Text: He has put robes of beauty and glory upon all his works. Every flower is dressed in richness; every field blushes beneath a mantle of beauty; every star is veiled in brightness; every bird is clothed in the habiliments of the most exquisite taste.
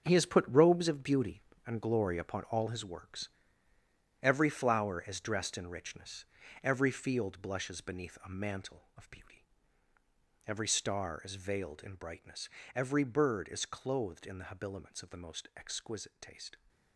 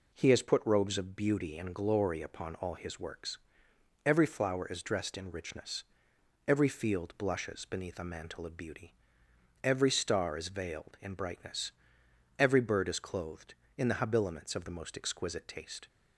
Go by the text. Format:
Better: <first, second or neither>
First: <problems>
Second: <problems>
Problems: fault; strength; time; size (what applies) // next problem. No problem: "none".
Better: second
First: gets quieter; strong; throughout; 10.5 dB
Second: none